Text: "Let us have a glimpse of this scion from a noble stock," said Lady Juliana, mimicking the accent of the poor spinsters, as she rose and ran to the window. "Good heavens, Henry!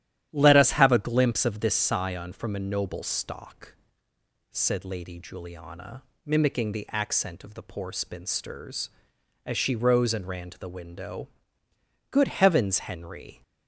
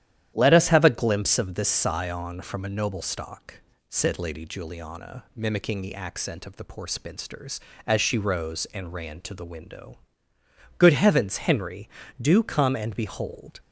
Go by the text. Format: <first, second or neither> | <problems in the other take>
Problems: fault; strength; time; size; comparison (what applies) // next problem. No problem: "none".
first | starts louder than the rest; strong; until 1.3 s; 11 dB; strong in the first // goes on to say "do come and behold"; from 12.1 s on; 1.4 s long